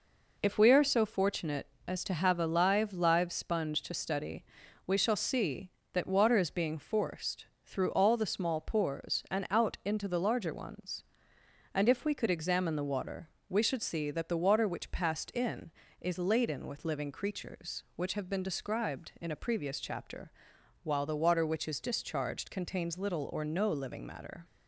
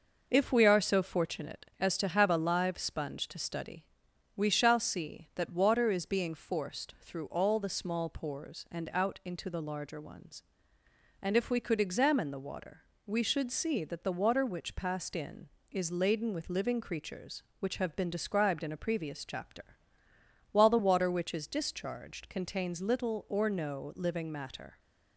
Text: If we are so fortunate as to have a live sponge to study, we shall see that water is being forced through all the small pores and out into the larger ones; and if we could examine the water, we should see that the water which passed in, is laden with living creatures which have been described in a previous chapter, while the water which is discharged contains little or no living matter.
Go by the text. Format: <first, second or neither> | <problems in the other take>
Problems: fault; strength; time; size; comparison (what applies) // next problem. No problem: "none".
second | says "live" twice; at 2.9 s // pauses between "forced" and "through"; slight; at 7.4 s; 0.20 s long